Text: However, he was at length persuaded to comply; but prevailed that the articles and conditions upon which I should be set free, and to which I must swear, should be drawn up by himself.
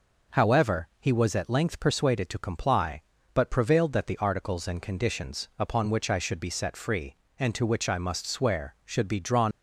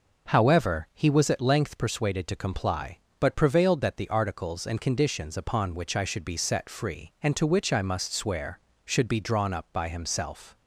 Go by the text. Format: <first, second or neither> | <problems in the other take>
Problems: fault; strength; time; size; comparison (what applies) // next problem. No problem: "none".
second | stops before "up by himself"; at 9.5 s